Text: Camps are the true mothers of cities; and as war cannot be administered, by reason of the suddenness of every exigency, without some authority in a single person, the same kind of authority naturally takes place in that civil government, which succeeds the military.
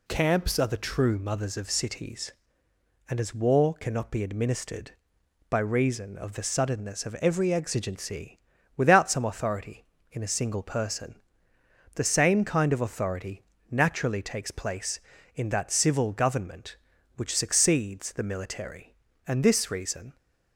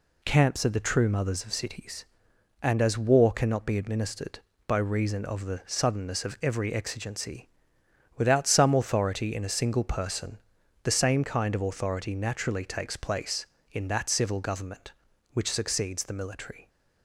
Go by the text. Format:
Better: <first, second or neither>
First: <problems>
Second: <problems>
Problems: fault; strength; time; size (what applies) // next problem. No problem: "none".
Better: second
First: pauses between "authority" and "naturally"; slight; at 13.4 s; 0.28 s long // goes on to say "And this reason"; noticeable; from 19.2 s on; 0.90 s long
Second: none